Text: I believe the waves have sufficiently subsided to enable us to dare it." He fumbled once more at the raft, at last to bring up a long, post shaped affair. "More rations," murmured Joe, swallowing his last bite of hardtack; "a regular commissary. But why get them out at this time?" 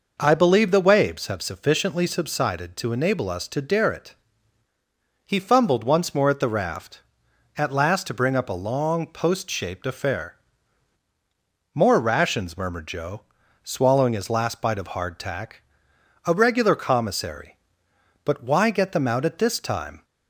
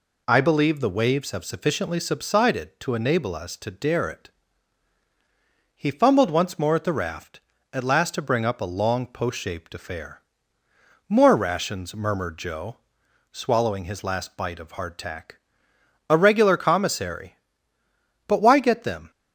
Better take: first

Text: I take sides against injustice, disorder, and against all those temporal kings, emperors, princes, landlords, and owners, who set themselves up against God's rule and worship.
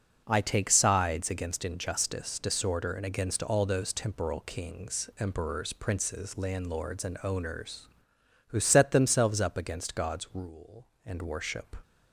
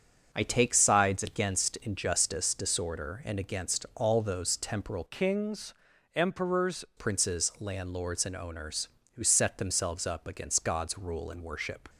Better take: first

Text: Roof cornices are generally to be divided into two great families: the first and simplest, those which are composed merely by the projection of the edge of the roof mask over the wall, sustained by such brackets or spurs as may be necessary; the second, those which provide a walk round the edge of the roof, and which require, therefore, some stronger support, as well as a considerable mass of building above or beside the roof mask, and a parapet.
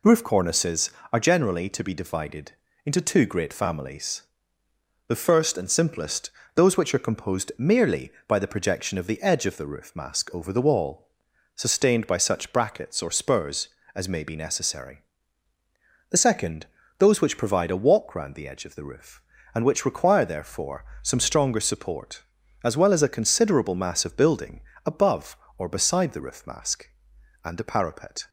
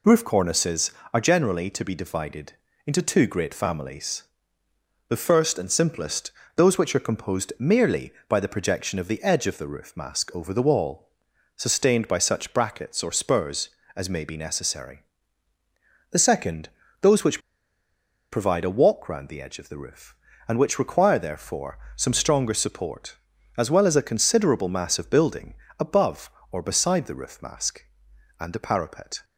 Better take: first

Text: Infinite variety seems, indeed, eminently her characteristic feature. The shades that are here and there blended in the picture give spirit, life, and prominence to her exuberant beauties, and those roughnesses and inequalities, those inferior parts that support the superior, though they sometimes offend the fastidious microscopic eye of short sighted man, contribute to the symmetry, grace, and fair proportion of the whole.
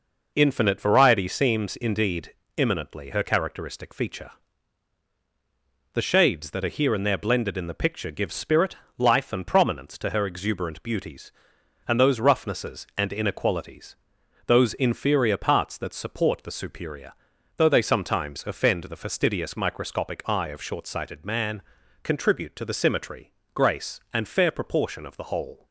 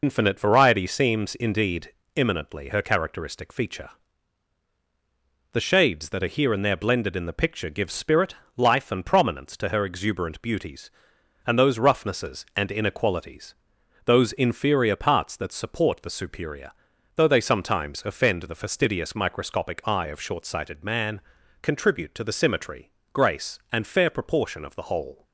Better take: first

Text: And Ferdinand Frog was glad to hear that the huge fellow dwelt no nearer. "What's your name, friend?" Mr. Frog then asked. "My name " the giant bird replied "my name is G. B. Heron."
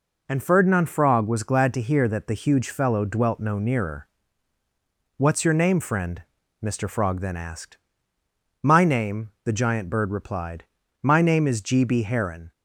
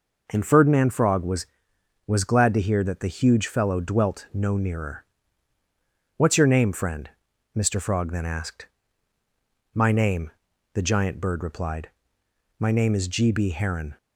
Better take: first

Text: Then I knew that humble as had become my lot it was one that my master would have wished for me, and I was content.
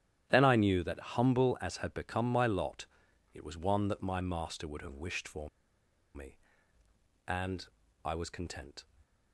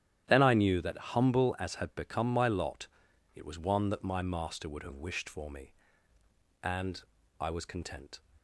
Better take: second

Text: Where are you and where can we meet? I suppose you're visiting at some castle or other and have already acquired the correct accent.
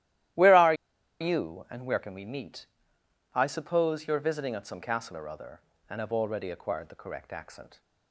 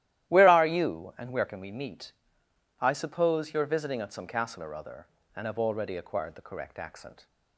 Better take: second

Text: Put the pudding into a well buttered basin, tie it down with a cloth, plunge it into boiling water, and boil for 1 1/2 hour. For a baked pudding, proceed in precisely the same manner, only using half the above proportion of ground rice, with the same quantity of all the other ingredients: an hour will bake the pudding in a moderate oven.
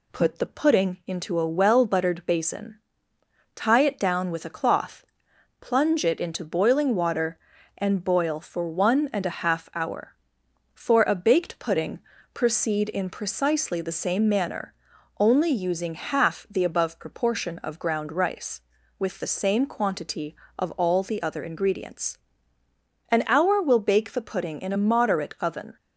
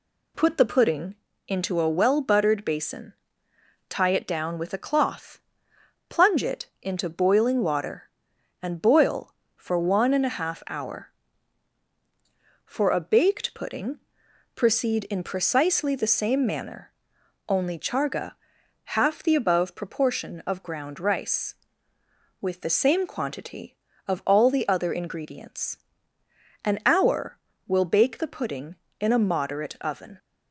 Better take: first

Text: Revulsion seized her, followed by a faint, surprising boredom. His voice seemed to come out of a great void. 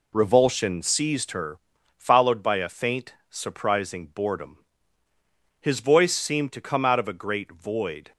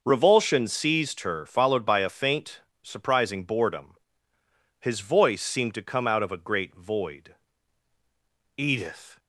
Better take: first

